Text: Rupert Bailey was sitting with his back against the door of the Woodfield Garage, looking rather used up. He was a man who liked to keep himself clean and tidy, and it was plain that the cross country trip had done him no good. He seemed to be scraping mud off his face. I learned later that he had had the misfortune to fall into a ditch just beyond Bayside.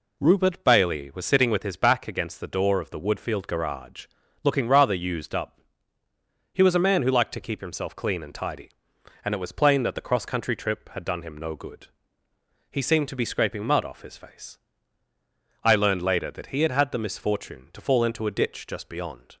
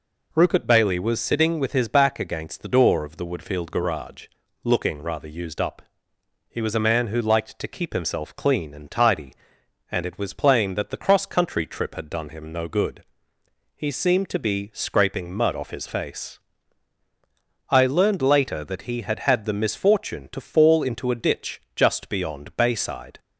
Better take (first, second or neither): second